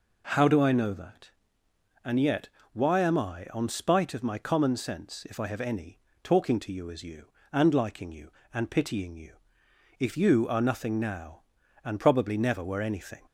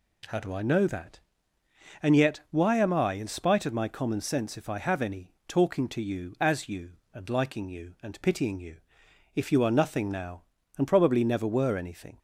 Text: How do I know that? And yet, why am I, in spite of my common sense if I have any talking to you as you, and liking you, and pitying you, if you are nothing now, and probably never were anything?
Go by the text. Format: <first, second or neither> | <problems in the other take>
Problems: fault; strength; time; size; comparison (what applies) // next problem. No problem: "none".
second | says "on" for "in"; at 3.5 s // pauses between "any" and "talking"; slight; at 5.9 s; 0.24 s long; slight in the second